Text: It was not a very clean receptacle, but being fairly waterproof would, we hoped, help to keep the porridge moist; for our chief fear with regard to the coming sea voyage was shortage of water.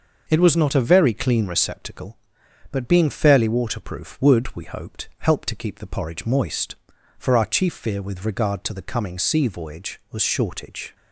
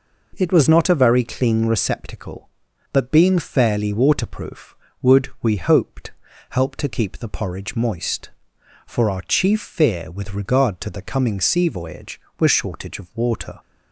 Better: second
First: stops before "of water"; at 10.9 s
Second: none

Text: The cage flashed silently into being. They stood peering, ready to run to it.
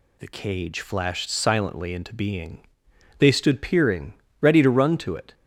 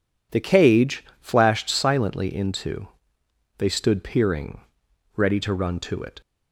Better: first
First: none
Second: pauses between "cage" and "flashed"; slight; at 1.0 s; 0.18 s long // skips "being"; at 3.2 s

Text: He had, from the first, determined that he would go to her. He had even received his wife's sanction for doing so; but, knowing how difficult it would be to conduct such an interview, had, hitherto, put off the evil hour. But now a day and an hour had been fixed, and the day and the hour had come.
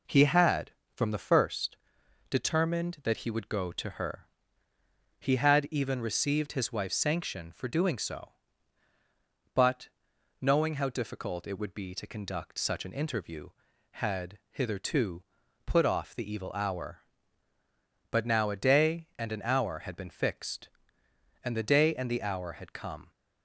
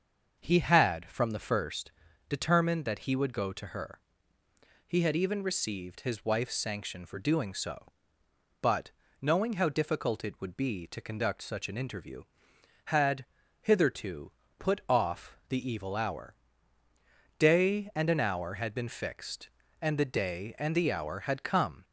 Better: first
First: none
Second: starts louder than the rest; until 1.4 s; 6.5 dB // skips "But now a"; at 16.8 s

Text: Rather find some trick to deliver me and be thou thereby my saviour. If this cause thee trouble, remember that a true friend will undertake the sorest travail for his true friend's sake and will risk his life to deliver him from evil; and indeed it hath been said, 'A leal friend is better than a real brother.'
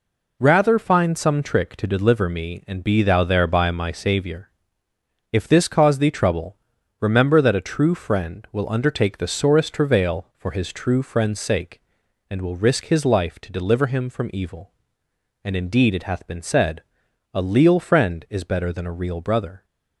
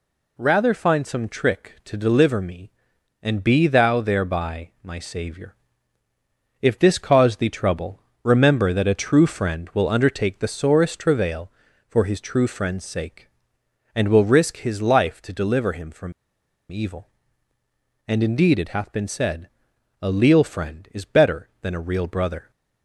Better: first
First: none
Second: pauses between "from" and "evil"; noticeable; at 16.1 s; 0.58 s long

